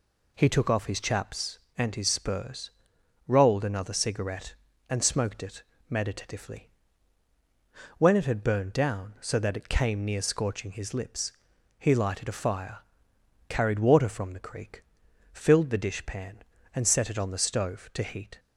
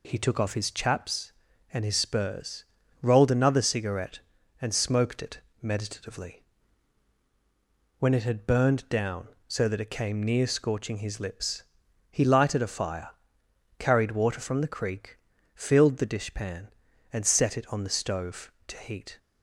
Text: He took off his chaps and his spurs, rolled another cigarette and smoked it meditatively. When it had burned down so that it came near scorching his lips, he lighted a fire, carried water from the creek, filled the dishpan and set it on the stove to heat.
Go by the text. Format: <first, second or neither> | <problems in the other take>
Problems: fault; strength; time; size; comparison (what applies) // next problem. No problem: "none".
neither | pauses between "it" and "meditatively"; slight; the same in both